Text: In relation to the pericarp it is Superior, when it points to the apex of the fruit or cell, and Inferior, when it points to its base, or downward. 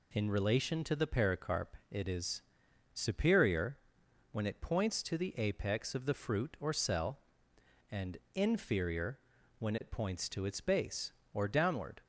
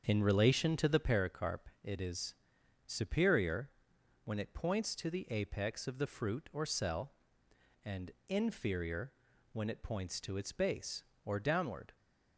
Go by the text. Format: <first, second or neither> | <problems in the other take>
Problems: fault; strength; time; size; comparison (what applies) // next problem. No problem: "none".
first | starts louder than the rest; until 1.2 s; 7 dB // pauses between "is" and "Superior"; noticeable; at 2.3 s; 0.52 s long; noticeable in the first // pauses between "and" and "Inferior"; slight; at 8.1 s; 0.16 s long; slight in the first